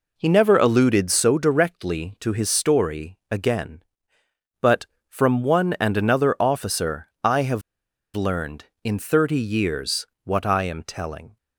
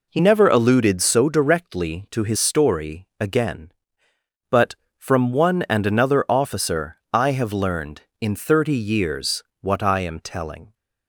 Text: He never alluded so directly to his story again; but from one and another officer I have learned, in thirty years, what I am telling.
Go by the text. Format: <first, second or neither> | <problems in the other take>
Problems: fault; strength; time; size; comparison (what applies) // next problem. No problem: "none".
second | pauses between "have" and "learned"; noticeable; at 7.6 s; 0.53 s long